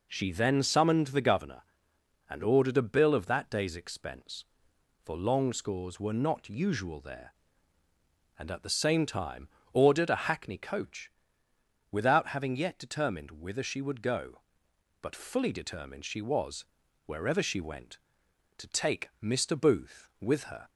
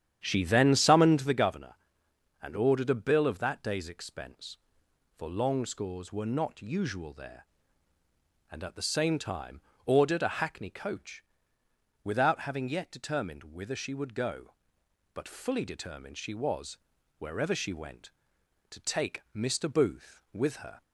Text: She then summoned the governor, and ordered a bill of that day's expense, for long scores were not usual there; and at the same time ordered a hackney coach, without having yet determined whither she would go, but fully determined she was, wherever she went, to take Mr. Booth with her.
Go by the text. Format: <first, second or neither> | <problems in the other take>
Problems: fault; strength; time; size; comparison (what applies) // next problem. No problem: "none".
first | starts louder than the rest; strong; until 1.4 s; 9.5 dB // pauses between "time" and "ordered"; slight; at 9.6 s; 0.24 s long; slight in the first